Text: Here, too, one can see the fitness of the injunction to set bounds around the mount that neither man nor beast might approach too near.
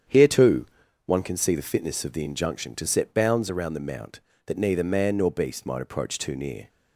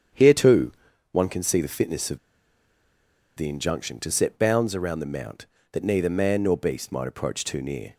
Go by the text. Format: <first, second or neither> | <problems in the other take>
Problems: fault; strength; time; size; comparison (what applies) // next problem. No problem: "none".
first | starts louder than the rest; strong; until 1.5 s; 8.5 dB; strong in the first // pauses between "of" and "the"; at 2.1 s; 1.1 s long